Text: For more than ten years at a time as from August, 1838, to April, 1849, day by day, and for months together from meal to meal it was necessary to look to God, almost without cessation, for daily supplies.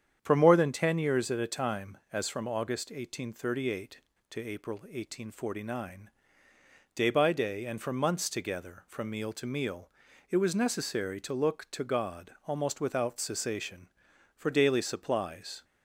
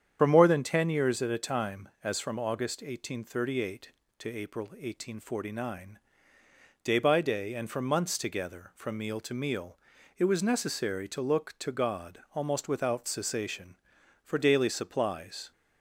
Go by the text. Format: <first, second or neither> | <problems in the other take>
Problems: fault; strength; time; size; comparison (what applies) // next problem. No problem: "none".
first | loses the start of "For"; at 0.1 s; 70 ms // starts louder than the rest; strong; until 1.2 s; 8.5 dB; strong in the first // pauses between "meal" and "it"; at 9.7 s; 0.40 s long; also in the first